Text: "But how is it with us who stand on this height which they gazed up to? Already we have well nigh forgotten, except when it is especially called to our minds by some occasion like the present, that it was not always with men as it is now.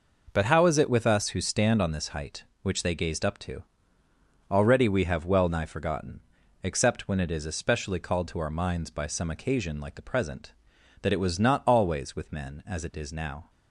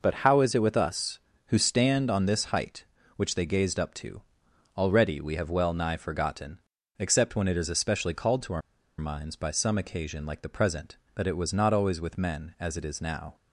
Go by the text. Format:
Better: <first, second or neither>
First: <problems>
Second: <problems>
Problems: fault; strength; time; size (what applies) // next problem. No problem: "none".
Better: first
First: none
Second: pauses between "our" and "minds"; at 8.6 s; 0.40 s long